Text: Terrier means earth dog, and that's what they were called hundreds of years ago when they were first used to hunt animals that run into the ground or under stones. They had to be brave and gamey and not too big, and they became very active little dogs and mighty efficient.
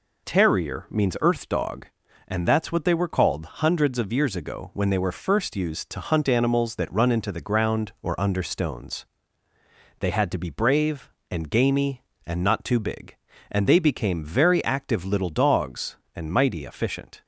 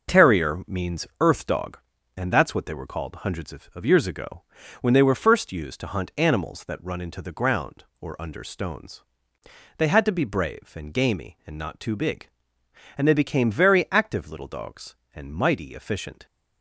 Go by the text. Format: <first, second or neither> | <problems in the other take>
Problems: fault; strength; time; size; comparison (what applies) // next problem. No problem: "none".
first | says "of" twice; at 3.7 s // pauses between "ago" and "when"; at 4.4 s; 0.40 s long